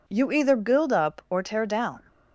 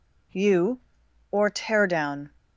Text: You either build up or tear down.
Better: first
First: none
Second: skips "either build up"; at 1.0 s

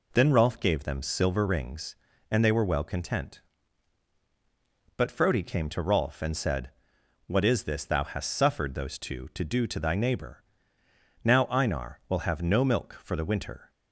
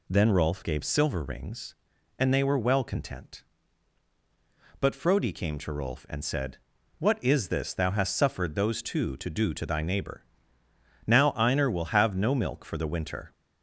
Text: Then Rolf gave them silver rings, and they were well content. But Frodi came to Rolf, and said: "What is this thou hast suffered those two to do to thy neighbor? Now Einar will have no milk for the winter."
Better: first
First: none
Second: skips "them"; at 0.8 s

